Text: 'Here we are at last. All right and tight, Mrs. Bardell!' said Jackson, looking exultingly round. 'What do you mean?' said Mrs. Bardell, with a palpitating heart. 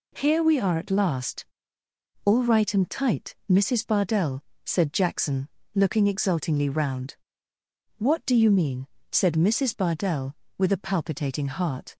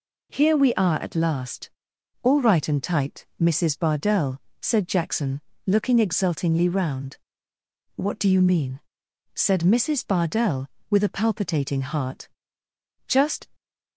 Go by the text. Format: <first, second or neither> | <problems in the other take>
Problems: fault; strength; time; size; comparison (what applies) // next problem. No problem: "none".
first | goes on to say "Just"; slight; from 13.0 s on; 0.40 s long